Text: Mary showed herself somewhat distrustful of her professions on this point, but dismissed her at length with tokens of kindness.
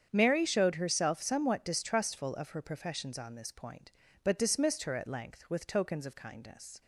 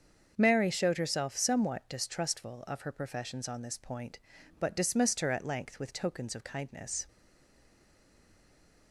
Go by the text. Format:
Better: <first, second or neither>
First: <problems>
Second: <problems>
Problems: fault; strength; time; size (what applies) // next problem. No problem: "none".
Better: first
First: starts louder than the rest; strong; until 1.1 s; 8 dB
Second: starts louder than the rest; until 1.3 s; 7 dB // stays silent after the last word; noticeable; from 7.0 s on; 1.9 s long